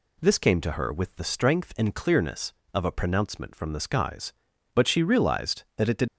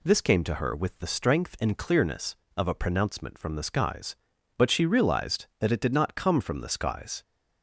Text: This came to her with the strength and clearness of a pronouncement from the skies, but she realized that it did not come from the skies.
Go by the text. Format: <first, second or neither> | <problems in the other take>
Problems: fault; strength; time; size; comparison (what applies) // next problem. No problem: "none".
second | stops before "not come from the skies"; at 6.0 s